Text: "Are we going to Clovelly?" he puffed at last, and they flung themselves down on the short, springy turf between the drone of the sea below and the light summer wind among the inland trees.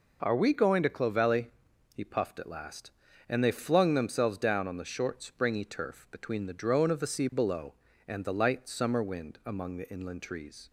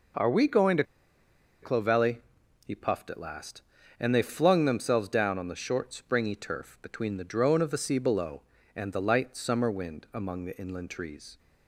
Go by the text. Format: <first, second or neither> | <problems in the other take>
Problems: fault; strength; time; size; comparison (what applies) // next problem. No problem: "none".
first | pauses between "to" and "Clovelly"; noticeable; at 0.8 s; 0.79 s long